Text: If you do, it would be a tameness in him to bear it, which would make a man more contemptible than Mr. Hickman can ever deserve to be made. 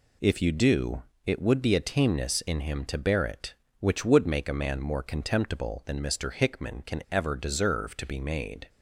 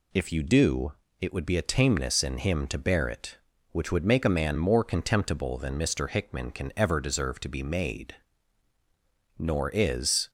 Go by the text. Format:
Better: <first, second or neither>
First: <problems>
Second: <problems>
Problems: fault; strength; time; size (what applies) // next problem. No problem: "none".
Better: first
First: none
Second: goes on to say "Nor is"; noticeable; from 9.3 s on; 0.92 s long